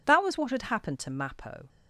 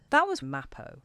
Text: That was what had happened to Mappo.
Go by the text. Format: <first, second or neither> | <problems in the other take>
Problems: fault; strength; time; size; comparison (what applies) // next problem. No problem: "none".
first | skips "what had happened to"; at 0.4 s